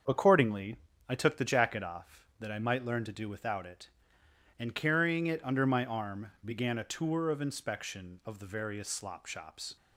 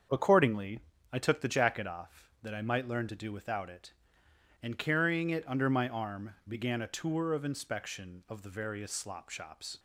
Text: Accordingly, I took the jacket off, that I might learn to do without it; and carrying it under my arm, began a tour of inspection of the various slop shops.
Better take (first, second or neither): neither